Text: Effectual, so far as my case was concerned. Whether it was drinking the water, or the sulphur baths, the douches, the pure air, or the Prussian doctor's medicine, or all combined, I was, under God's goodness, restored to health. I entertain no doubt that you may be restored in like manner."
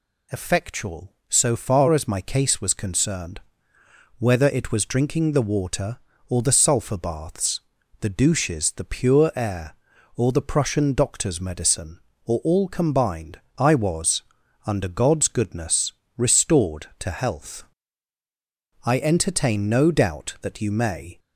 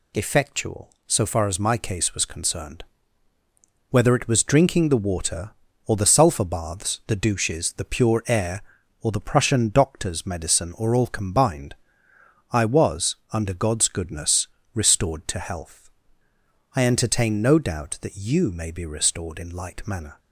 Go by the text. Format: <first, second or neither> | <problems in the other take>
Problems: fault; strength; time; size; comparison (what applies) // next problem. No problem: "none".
second | stops before "be restored in like manner"; at 21.1 s